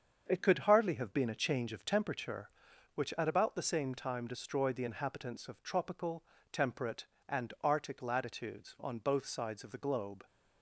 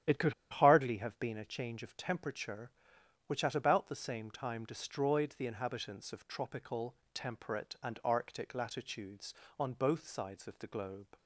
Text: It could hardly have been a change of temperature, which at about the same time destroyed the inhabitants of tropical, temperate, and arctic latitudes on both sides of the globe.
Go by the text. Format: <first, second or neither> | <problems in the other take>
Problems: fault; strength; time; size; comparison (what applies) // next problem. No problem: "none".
first | starts louder than the rest; strong; until 1.2 s; 10.5 dB; strong in the first // pauses between "could" and "hardly"; slight; at 0.3 s; 0.17 s long